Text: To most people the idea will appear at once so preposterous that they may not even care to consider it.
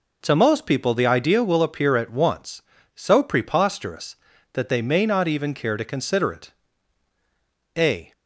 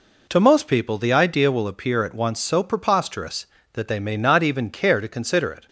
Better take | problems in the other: second | goes on to say "A"; slight; from 7.7 s on; 0.36 s long

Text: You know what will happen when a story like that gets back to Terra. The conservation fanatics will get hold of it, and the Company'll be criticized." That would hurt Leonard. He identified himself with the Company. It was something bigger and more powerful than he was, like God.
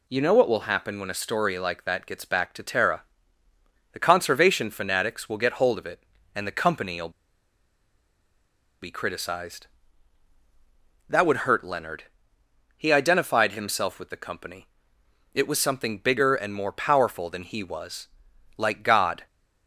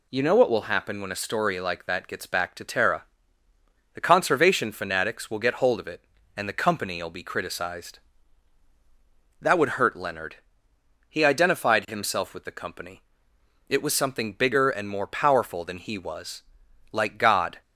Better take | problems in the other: second | pauses between "Company'll" and "be"; strong; at 7.1 s; 1.7 s long

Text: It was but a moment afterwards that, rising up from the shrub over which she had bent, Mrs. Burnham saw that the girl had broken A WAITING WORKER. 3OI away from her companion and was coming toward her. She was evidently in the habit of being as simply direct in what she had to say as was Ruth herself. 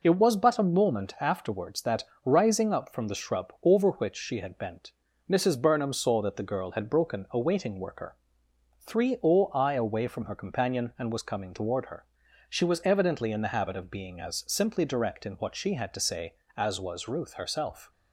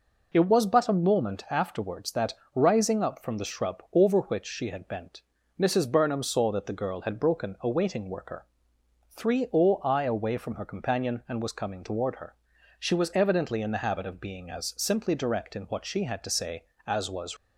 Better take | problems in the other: first | stops before "Ruth herself"; at 17.3 s

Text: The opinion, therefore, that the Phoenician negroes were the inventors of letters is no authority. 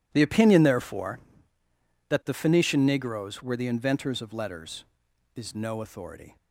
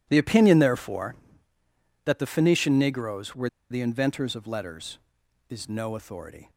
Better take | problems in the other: first | pauses between "were" and "the"; slight; at 3.4 s; 0.21 s long

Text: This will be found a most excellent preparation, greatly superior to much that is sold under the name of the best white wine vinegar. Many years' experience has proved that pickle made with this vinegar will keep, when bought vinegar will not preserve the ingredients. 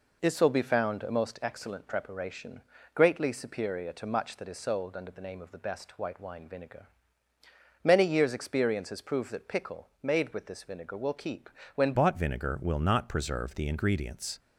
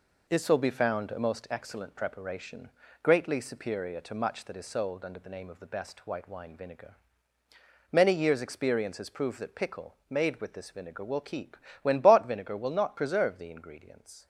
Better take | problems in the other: second | pauses between "pickle" and "made"; slight; at 9.8 s; 0.16 s long; slight in the second // changes voice at "bought"; from 11.9 s on; 2.4 s long

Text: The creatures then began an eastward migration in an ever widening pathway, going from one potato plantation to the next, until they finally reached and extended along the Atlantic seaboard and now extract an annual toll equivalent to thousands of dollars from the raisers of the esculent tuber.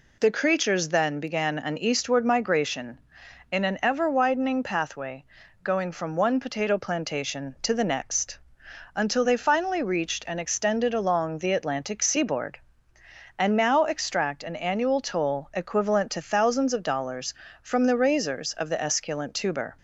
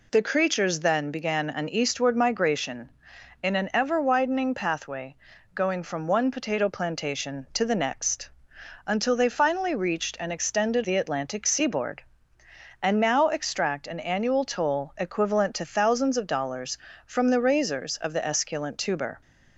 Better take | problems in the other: first | skips "along"; at 10.8 s

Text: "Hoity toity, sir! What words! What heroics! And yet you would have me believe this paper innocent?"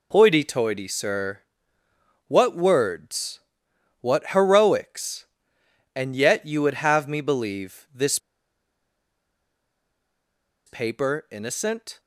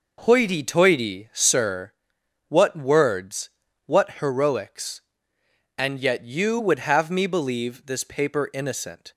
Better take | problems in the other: second | pauses between "this" and "paper"; strong; at 8.1 s; 2.4 s long

